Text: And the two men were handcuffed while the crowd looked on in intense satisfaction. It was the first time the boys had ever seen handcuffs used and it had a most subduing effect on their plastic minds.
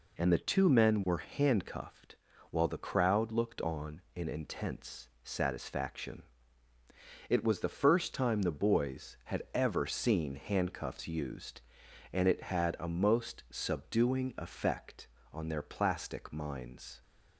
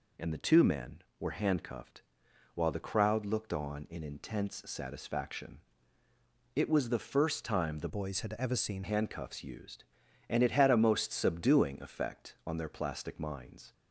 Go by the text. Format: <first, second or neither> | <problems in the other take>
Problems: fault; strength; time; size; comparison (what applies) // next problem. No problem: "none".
first | pauses between "handcuffed" and "while"; noticeable; at 2.0 s; 0.54 s long; slight in the first // changes voice from "boys" to "seen"; from 7.8 to 8.8 s; 1.0 s long